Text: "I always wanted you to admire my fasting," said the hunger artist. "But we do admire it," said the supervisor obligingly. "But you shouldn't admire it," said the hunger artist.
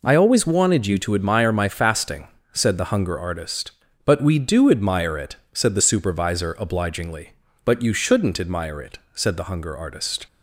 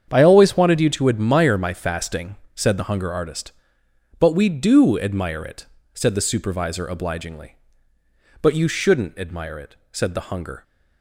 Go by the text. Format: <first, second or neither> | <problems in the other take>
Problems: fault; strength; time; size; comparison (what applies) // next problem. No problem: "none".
first | starts louder than the rest; strong; until 1.1 s; 8 dB // stops before "artist"; at 10.6 s